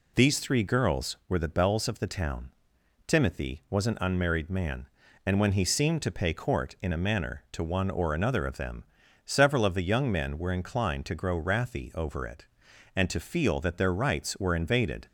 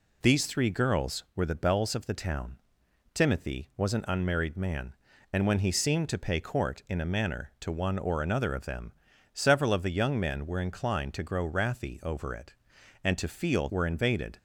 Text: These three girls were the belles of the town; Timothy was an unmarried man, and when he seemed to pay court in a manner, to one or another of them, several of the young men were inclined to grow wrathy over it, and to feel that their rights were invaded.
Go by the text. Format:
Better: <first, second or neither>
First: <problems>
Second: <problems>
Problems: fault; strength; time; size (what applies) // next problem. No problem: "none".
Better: first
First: none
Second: skips "that their rights"; at 13.6 s